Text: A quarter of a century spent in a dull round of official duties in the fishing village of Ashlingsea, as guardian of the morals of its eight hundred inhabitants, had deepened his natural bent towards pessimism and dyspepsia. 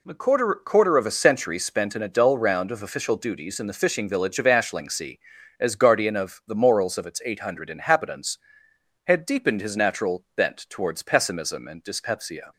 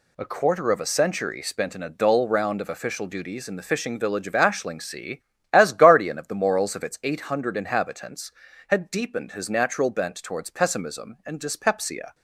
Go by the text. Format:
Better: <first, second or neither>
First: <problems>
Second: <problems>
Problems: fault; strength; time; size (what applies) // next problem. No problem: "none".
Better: second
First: says "quarter" twice; at 0.6 s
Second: none